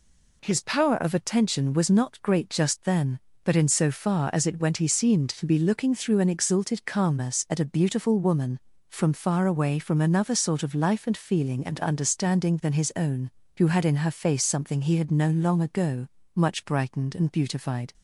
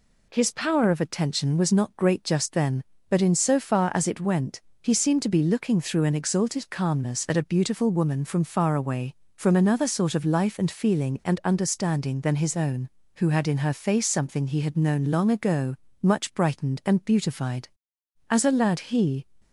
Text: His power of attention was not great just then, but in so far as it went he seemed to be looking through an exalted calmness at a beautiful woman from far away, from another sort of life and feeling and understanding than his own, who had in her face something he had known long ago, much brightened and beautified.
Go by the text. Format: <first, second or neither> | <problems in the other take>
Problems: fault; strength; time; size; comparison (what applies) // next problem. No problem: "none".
first | pauses between "went" and "he"; slight; at 4.6 s; 0.22 s long // goes on to say "As a lad he"; noticeable; from 18.3 s on; 0.96 s long